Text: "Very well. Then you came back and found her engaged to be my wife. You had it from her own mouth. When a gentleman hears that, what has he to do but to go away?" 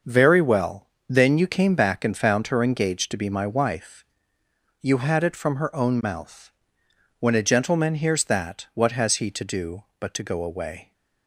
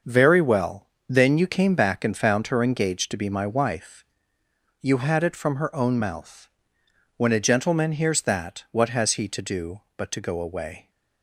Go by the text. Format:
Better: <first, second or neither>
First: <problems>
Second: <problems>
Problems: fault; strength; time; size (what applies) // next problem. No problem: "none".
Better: neither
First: starts louder than the rest; until 1.2 s; 6 dB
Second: starts louder than the rest; until 1.2 s; 6 dB